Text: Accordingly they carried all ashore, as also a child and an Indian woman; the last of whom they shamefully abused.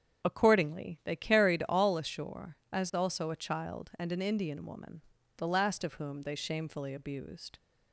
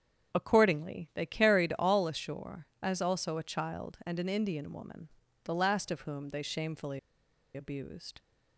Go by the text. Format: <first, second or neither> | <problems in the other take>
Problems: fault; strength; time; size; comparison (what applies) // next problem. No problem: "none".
first | starts louder than the rest; strong; until 1.4 s; 7.5 dB; strong in the first // pauses between "shamefully" and "abused"; noticeable; at 6.9 s; 0.56 s long